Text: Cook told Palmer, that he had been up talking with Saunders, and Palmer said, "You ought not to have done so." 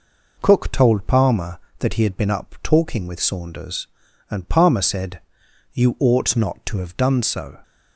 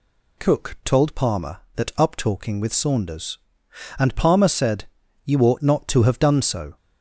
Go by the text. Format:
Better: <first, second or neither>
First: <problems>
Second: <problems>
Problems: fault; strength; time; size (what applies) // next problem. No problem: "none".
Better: first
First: none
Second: skips "he had been"; at 1.9 s